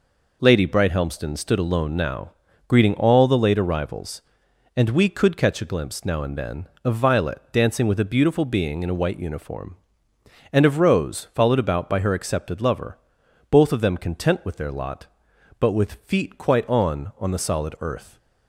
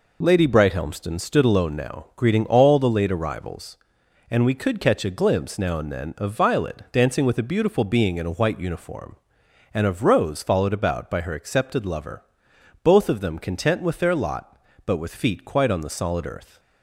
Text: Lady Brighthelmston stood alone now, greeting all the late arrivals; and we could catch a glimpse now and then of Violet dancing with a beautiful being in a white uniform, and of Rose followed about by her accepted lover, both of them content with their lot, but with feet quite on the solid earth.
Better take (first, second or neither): second